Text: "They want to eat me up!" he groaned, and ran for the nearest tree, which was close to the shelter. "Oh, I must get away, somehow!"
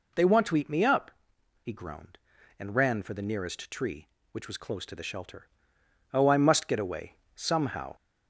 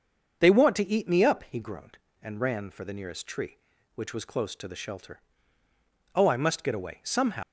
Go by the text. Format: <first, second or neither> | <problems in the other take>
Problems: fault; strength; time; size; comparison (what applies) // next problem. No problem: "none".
first | starts louder than the rest; until 1.4 s; 6.5 dB // leaves "somehow" unfinished; at 7.4 s; 105 ms